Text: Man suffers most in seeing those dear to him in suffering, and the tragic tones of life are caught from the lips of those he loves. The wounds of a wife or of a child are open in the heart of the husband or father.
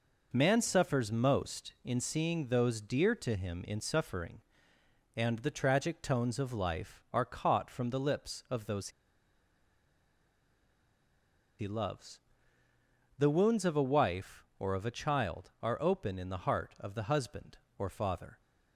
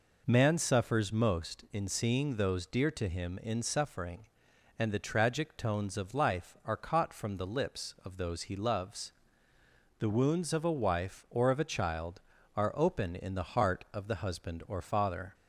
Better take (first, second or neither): second